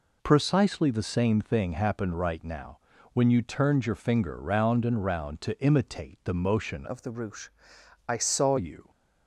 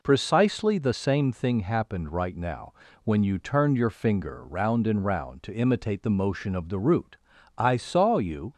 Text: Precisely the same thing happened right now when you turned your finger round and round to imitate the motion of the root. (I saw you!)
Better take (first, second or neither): second